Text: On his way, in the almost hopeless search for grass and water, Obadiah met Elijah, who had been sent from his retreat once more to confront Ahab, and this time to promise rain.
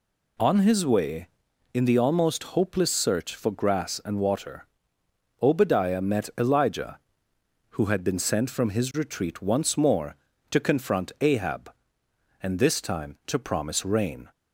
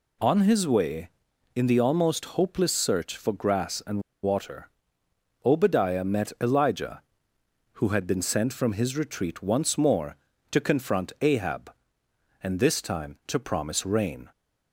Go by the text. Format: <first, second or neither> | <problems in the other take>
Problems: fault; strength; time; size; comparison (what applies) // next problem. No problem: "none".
first | pauses between "and" and "water"; slight; at 4.0 s; 0.22 s long